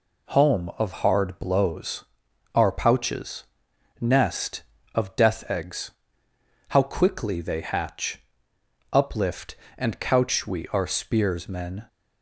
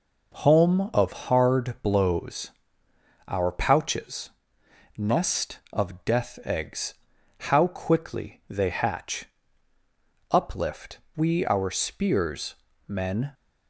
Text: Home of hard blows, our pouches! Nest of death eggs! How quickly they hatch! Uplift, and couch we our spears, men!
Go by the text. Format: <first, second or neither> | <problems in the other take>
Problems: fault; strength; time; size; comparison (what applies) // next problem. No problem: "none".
first | skips "and couch"; at 11.0 s